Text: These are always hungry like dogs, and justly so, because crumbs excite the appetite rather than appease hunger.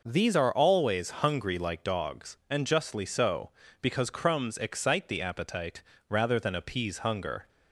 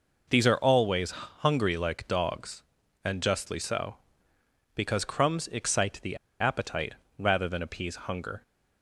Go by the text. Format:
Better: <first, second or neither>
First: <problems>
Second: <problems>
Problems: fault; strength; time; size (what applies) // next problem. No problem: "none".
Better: first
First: pauses between "appetite" and "rather"; slight; at 5.8 s; 0.26 s long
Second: pauses between "always" and "hungry"; slight; at 1.1 s; 0.28 s long // pauses between "the" and "appetite"; slight; at 6.1 s; 0.22 s long // pauses between "appetite" and "rather"; slight; at 6.9 s; 0.24 s long